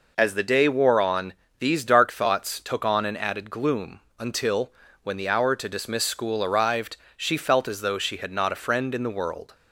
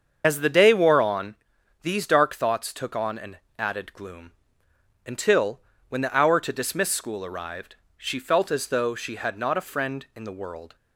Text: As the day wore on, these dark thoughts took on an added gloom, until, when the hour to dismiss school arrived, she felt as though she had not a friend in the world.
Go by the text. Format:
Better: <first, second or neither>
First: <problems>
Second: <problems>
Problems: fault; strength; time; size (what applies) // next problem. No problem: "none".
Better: first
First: none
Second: loses the start of "As"; at 0.2 s; 35 ms // starts louder than the rest; until 1.2 s; 7 dB // pauses between "an" and "added"; slight; at 3.3 s; 0.20 s long